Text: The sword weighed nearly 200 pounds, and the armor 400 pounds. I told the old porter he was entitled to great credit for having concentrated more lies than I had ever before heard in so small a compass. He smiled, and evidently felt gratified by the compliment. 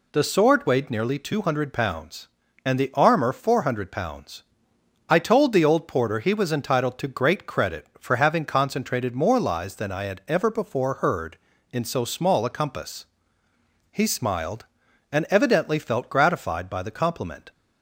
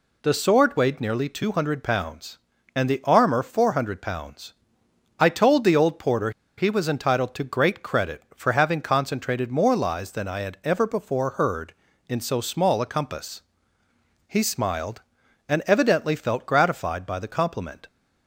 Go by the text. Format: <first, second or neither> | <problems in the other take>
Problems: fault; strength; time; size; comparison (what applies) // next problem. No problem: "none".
first | pauses between "porter" and "he"; slight; at 6.2 s; 0.27 s long